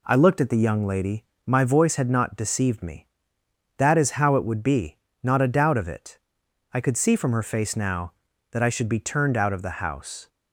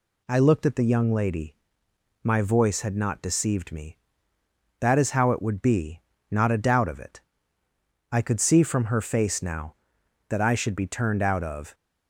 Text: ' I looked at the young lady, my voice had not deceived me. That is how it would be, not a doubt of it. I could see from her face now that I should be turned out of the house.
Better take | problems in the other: first | stops before "the house"; at 11.7 s

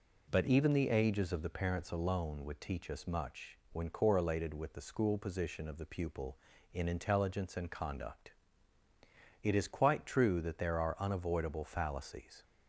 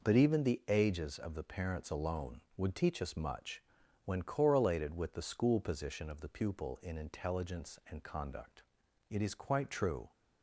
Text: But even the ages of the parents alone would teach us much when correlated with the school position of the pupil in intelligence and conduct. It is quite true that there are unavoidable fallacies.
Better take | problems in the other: first | pauses between "much" and "when"; at 3.6 s; 0.42 s long; slight in the first // stops before "that there are unavoidable fallacies"; at 10.1 s

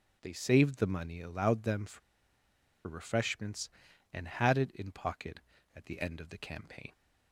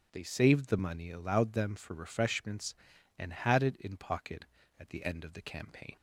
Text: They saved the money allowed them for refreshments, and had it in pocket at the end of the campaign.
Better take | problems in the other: second | starts louder than the rest; strong; until 1.2 s; 7.5 dB; strong in the second // pauses between "for" and "refreshments"; noticeable; at 2.0 s; 0.87 s long

